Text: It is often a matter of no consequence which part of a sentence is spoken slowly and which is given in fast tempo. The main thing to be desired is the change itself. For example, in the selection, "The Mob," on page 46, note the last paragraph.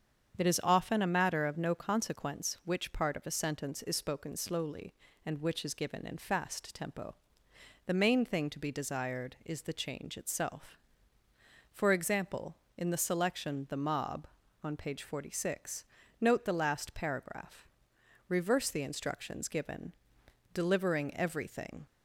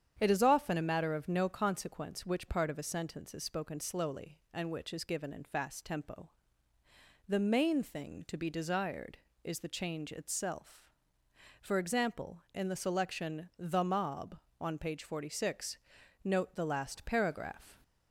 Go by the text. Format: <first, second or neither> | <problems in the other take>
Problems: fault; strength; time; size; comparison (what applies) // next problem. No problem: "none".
second | starts louder than the rest; strong; until 1.4 s; 7.5 dB; strong in the second // goes on to say "Reverse the instructions given delivering everything"; strong; from 18.2 s on; 3.5 s long